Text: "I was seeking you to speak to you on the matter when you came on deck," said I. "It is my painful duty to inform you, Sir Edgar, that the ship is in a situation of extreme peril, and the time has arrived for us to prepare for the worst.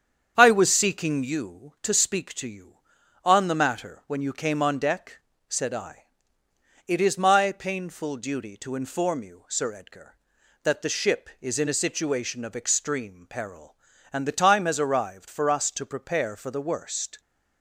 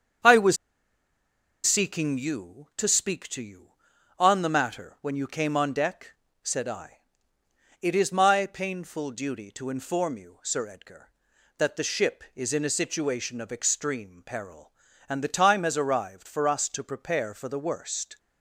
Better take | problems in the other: first | starts louder than the rest; strong; until 2.3 s; 7.5 dB; strong in the first // pauses between "was" and "seeking"; at 0.5 s; 1.0 s long

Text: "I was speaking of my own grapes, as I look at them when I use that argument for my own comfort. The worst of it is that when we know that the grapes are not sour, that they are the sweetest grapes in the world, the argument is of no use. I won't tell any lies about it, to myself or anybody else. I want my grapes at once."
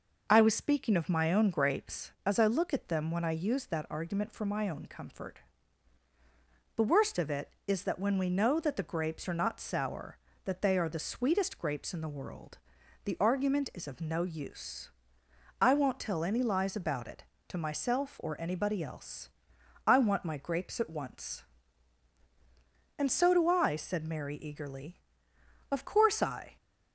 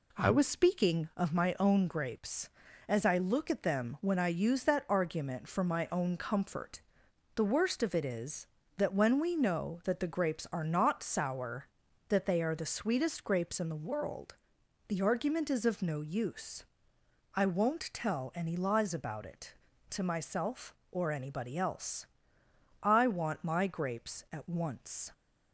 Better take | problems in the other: second | goes on to say "And so do I said Mary eagerly of course I"; strong; from 22.9 s on; 3.5 s long

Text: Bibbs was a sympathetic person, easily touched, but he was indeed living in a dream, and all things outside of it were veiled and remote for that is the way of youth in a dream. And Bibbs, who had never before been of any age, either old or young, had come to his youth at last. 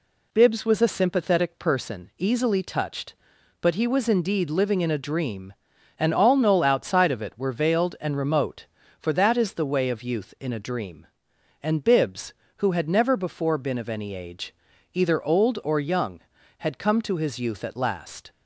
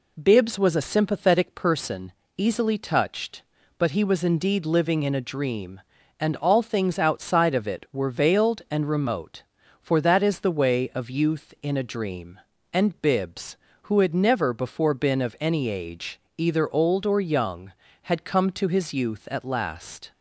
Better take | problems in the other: second | says "knoll" for "things"; at 6.3 s

